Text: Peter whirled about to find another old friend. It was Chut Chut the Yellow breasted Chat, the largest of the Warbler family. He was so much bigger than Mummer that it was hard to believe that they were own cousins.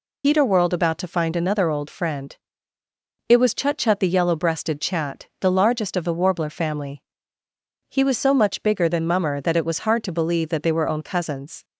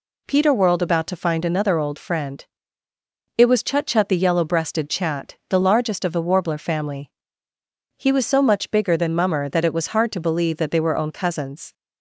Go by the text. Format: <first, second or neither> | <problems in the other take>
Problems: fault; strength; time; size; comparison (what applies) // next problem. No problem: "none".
second | loses the start of "Peter"; at 0.2 s; 80 ms